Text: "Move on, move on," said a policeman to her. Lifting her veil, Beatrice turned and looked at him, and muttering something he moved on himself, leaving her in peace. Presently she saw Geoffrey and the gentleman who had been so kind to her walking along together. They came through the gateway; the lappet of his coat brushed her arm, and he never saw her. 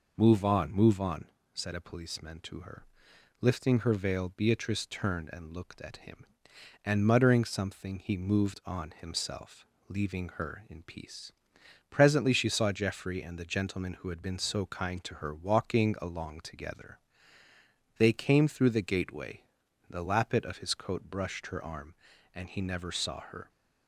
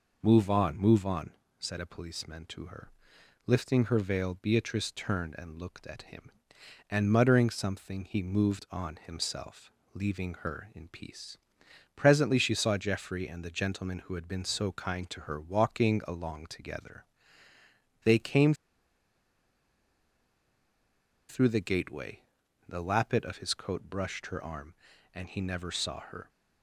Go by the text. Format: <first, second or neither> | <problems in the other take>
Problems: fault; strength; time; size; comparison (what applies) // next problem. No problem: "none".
first | pauses between "came" and "through"; strong; at 18.5 s; 2.7 s long